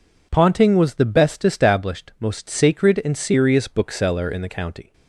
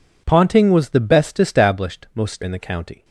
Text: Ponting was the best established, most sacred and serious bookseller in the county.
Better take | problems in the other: first | skips "sacred and serious bookseller"; at 2.4 s

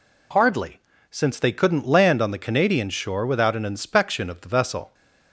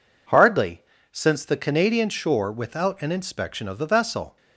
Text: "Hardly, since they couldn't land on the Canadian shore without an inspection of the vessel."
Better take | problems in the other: first | skips "they couldn't land on"; at 1.4 s

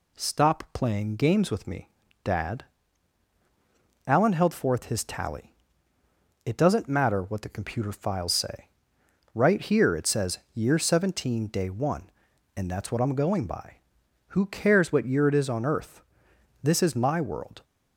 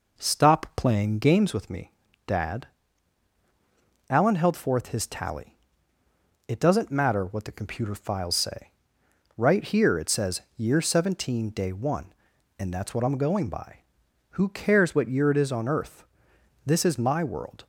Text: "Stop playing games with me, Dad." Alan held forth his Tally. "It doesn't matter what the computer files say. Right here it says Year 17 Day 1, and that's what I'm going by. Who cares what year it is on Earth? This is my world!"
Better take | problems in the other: first | starts louder than the rest; noticeable; until 1.5 s; 5 dB // pauses between "says" and "Year"; slight; at 10.4 s; 0.16 s long; slight in the first

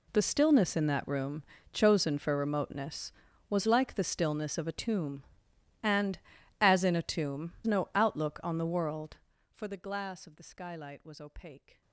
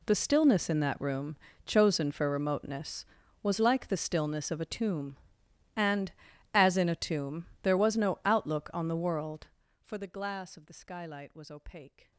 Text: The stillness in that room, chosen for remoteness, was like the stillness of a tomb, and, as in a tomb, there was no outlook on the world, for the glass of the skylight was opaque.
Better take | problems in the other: second | skips "there was"; at 7.5 s

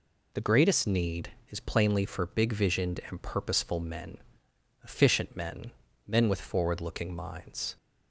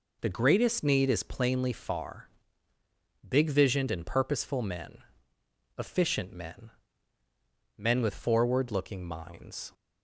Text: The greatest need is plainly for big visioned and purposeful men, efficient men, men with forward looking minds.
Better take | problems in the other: first | says "far" for "for"; at 1.7 s

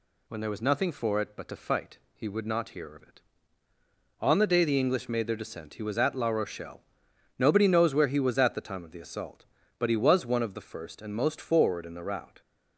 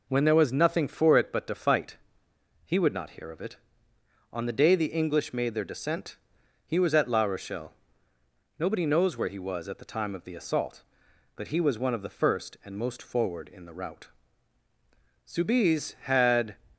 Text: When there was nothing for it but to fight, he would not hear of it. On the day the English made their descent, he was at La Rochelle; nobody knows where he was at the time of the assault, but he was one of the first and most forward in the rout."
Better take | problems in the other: first | goes on to say "Soubise had"; noticeable; from 15.2 s on; 1.3 s long

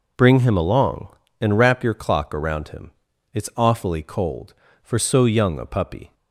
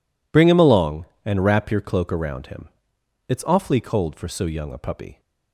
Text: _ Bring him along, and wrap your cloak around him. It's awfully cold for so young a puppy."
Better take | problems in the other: second | says "clock" for "cloak"; at 1.9 s

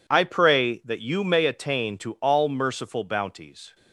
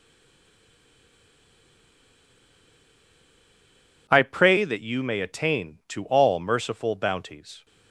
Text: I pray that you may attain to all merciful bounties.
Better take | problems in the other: first | stays silent before the first word; strong; until 4.0 s; 4.0 s long

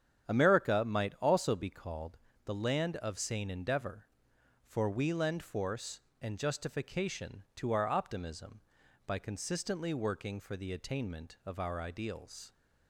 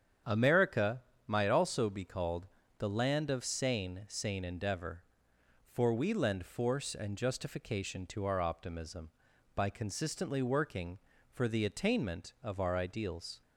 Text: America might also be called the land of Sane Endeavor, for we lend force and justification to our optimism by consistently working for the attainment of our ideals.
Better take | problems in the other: first | starts louder than the rest; strong; until 1.5 s; 8.5 dB; strong in the first // pauses between "America" and "might"; slight; at 1.0 s; 0.26 s long // pauses between "called" and "the"; slight; at 2.4 s; 0.30 s long; slight in the first // says "Sane" twice; at 4.0 s

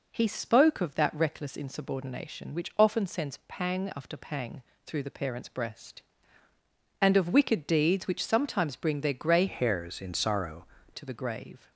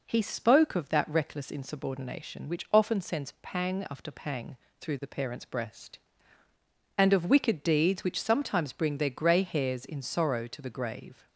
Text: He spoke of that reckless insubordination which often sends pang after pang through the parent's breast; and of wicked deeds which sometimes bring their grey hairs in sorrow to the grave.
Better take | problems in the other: second | pauses between "pang" and "through"; slight; at 4.6 s; 0.24 s long; slight in the second // changes voice from "hairs" to "sorrow"; from 9.4 to 10.6 s; 1.2 s long

